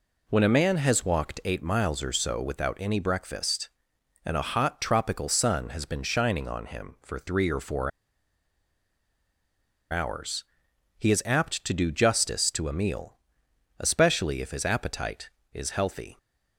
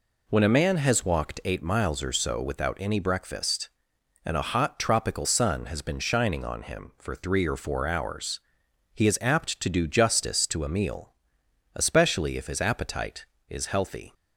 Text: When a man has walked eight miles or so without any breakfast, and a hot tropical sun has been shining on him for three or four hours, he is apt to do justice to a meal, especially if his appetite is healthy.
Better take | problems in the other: second | pauses between "four" and "hours"; strong; at 7.9 s; 2.0 s long

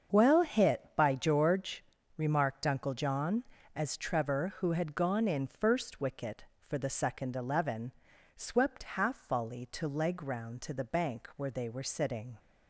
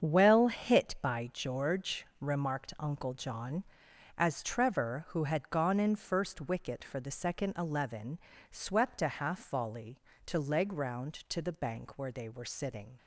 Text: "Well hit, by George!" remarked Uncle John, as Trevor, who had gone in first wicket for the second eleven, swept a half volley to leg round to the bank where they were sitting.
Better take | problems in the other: second | starts louder than the rest; until 1.2 s; 7 dB; strong in the second // skips "a"; at 8.9 s

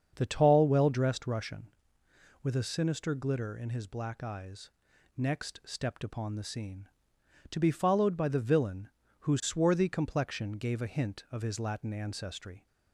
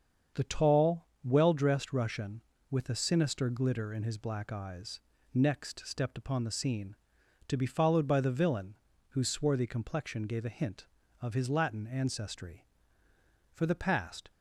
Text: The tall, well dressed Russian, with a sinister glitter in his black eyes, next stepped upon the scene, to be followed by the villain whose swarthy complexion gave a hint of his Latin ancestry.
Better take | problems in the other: first | starts louder than the rest; strong; until 1.5 s; 7 dB; also in the first // pauses between "villain" and "whose"; slight; at 8.7 s; 0.34 s long; slight in the first // goes on to say "For the past"; noticeable; from 13.5 s on; 0.78 s long

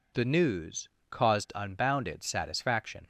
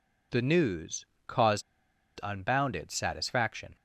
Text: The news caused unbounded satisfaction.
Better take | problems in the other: first | pauses between "news" and "caused"; slight; at 1.0 s; 0.20 s long; slight in the first // pauses between "caused" and "unbounded"; noticeable; at 1.6 s; 0.61 s long

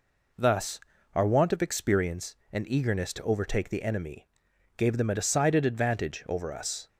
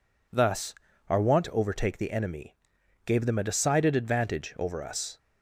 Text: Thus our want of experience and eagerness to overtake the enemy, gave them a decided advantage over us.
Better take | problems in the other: first | pauses between "Thus" and "our"; slight; at 0.7 s; 0.34 s long; slight in the first // skips "of experience and eagerness"; at 1.4 s

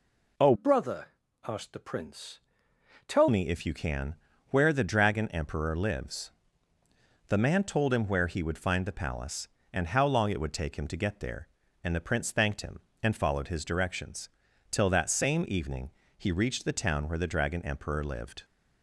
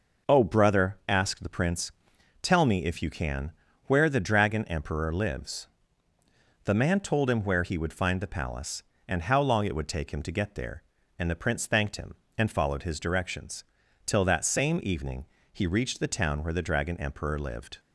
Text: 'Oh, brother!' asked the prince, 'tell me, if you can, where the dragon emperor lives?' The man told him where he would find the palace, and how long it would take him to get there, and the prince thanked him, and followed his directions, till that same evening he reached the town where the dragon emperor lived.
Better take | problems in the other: second | changes voice from "brother" to "tell"; from 0.5 to 3.2 s; 2.7 s long // pauses between "evening" and "he"; slight; at 15.9 s; 0.26 s long; slight in the second

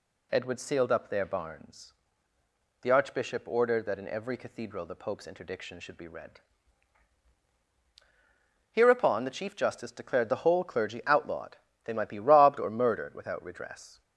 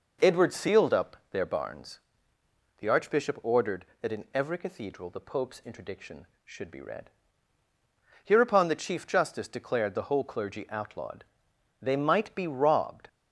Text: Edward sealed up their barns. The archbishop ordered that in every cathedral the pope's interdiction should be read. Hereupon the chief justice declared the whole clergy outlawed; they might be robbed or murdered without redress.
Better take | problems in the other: first | pauses between "up" and "their"; slight; at 1.1 s; 0.16 s long // stops before "or murdered without redress"; at 13.0 s

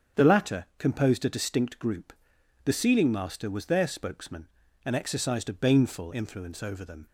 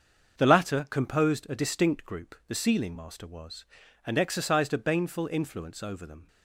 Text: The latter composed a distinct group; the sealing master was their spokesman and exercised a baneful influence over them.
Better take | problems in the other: first | starts louder than the rest; until 1.4 s; 6.5 dB; strong in the first // skips "their spokesman"; at 3.8 s

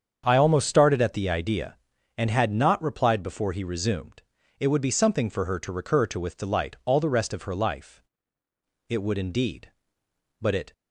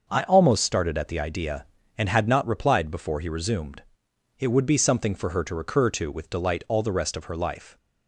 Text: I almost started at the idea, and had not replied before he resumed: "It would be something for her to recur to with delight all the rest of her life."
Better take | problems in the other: second | starts louder than the rest; strong; until 1.2 s; 7.5 dB; noticeable in the second // goes on to say "It would indeed But it"; strong; from 8.8 s on; 1.8 s long

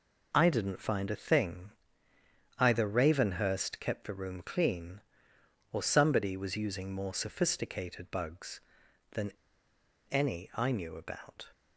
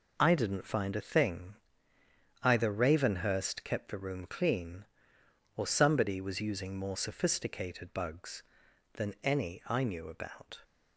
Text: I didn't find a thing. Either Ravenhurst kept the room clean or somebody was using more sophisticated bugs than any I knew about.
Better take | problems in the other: second | pauses between "than" and "any"; noticeable; at 9.3 s; 0.80 s long

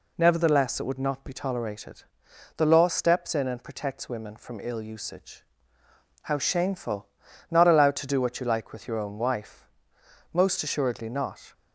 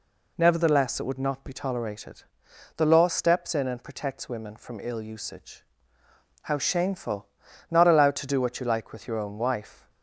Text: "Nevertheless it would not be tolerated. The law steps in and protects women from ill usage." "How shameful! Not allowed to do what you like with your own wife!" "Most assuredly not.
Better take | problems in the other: first | stops before "Most assuredly not"; at 9.8 s

